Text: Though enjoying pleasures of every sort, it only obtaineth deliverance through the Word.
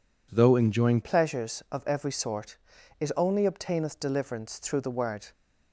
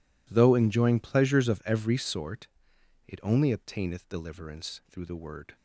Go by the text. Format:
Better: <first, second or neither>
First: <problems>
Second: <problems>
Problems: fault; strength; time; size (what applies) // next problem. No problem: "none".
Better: second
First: changes voice at "pleasures"; from 1.0 s on; 4.3 s long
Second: none